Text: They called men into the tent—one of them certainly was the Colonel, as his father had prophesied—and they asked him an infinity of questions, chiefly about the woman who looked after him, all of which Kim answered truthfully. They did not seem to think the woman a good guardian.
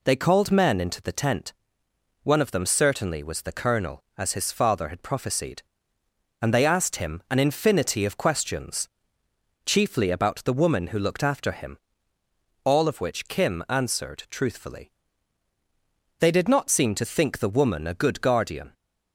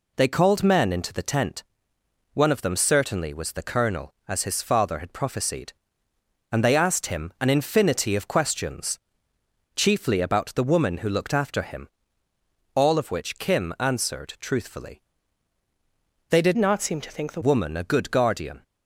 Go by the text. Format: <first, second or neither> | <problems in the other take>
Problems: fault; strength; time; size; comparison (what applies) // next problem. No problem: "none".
first | changes voice from "not" to "the"; from 16.5 to 17.3 s; 0.8 s long